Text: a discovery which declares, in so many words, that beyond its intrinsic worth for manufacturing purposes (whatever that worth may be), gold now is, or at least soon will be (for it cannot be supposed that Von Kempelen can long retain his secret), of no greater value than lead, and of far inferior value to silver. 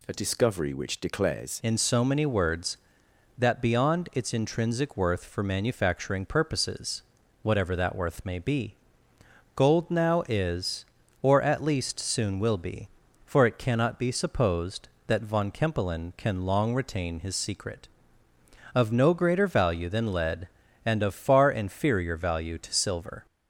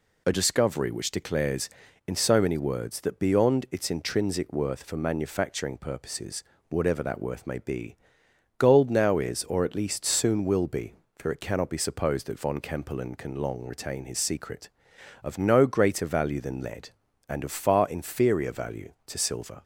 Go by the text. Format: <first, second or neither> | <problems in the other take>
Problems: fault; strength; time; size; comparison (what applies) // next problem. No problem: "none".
second | changes voice at "in"; from 1.6 s on; 21.6 s long